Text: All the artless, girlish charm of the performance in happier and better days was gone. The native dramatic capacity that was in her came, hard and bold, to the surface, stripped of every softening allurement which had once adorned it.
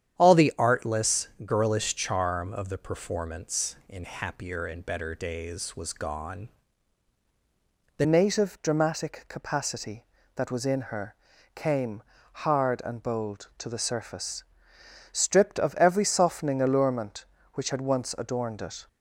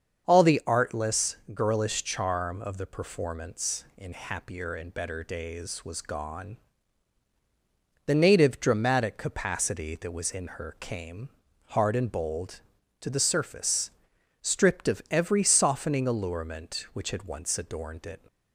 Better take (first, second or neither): second